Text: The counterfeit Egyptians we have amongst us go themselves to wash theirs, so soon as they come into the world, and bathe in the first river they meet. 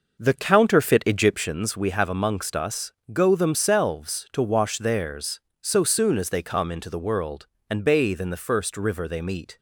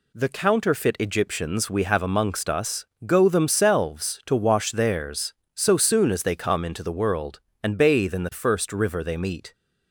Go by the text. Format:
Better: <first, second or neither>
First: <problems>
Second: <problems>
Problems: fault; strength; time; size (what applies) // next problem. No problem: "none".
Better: second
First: starts louder than the rest; noticeable; until 1.6 s; 6 dB // pauses between "us" and "go"; slight; at 2.9 s; 0.18 s long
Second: pauses between "us" and "go"; slight; at 2.8 s; 0.18 s long